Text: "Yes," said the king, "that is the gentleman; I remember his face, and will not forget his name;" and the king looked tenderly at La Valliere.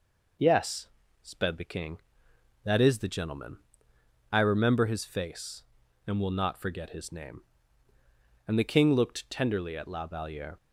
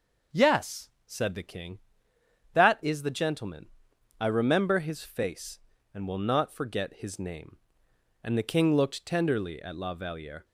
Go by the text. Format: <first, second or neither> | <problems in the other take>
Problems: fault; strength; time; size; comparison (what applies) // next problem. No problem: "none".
second | says "sped" for "said"; at 1.2 s